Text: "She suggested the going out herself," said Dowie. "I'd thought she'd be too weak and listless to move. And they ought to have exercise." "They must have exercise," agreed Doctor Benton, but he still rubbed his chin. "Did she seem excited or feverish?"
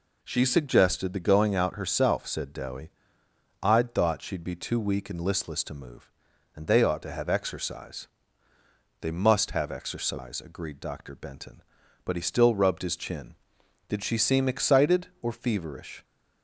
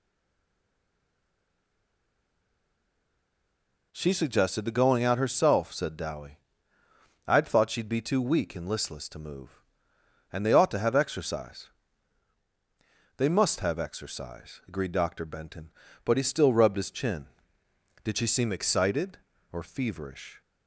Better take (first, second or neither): first